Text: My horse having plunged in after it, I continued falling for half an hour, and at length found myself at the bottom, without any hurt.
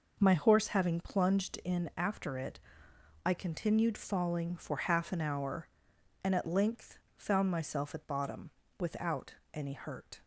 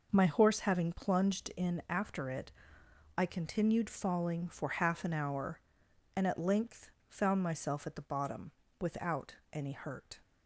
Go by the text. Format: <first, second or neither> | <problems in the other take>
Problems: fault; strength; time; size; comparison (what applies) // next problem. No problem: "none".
second | pauses between "length" and "found"; slight; at 6.9 s; 0.18 s long; slight in the second // skips "the"; at 8.0 s // pauses between "without" and "any"; slight; at 9.3 s; 0.18 s long; slight in the second